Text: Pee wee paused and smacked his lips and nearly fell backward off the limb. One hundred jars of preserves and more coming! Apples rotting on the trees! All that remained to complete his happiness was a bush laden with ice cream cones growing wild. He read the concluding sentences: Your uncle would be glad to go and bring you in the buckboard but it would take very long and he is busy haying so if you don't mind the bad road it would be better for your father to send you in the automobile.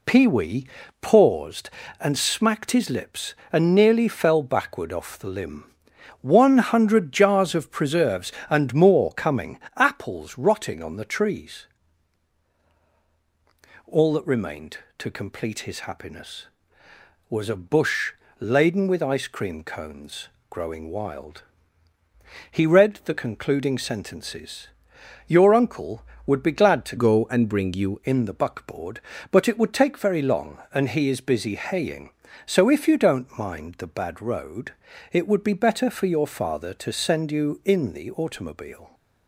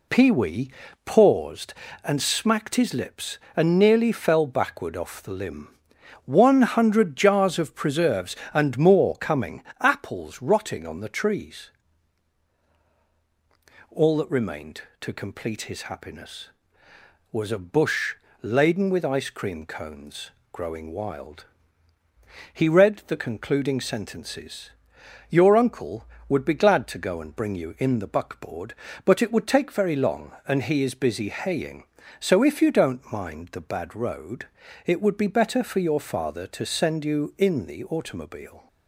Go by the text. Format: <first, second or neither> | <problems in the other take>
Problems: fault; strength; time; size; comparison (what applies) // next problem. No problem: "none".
second | pauses between "wee" and "paused"; slight; at 0.6 s; 0.34 s long; slight in the second // pauses between "bush" and "laden"; slight; at 18.1 s; 0.26 s long; slight in the second // pauses between "cones" and "growing"; slight; at 20.2 s; 0.22 s long; slight in the second // changes voice from "go" to "you"; from 26.9 to 28.0 s; 1.1 s long // pauses between "road" and "it"; at 34.7 s; 0.40 s long; also in the second